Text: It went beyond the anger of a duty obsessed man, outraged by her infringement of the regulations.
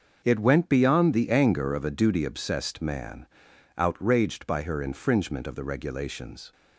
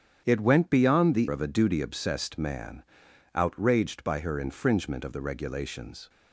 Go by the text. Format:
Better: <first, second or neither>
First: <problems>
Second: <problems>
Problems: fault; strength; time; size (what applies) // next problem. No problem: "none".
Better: first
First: starts louder than the rest; until 1.2 s; 6 dB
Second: starts louder than the rest; strong; until 1.2 s; 8.5 dB // skips "anger"; at 1.2 s